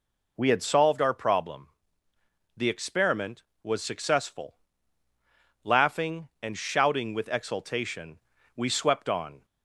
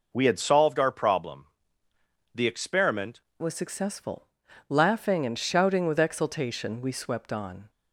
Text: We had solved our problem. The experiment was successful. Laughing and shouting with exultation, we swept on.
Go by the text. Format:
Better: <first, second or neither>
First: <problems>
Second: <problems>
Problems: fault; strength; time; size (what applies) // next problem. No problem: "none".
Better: first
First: none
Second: changes voice at "was"; from 3.4 s on; 4.2 s long